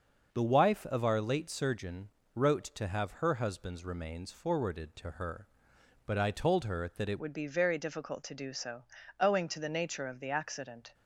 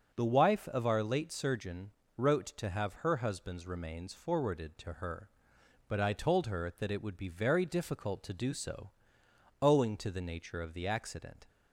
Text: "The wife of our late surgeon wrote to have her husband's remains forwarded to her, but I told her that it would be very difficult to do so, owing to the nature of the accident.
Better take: second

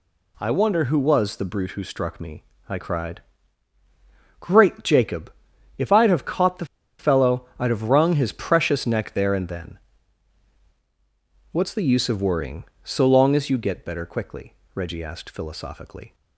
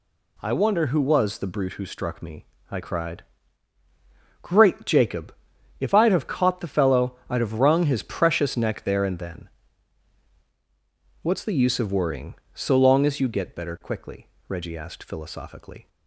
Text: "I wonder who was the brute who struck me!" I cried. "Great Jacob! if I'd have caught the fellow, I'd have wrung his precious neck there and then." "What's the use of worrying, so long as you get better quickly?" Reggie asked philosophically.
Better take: second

